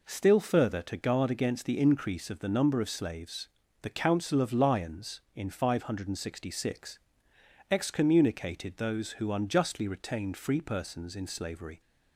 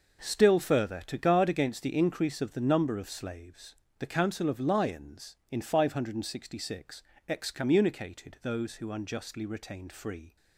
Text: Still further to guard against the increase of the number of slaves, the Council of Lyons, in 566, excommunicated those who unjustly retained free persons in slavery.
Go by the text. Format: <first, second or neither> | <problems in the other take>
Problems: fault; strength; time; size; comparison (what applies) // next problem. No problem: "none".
first | stops before "persons in slavery"; at 10.3 s